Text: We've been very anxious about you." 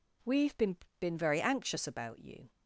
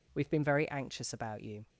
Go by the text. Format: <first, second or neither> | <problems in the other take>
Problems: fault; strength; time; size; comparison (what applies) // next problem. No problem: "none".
second | says "been" twice; at 1.0 s